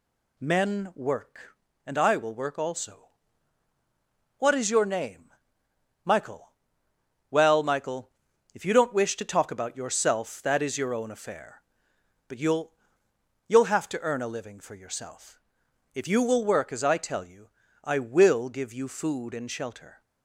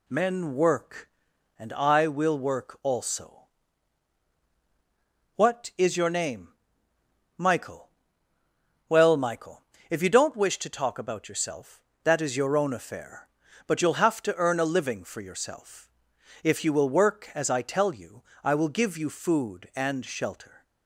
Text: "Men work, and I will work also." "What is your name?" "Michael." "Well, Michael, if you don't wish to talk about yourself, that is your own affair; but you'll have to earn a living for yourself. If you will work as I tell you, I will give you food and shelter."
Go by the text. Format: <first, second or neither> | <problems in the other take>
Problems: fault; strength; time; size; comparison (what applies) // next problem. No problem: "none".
second | says "you'll" twice; at 13.4 s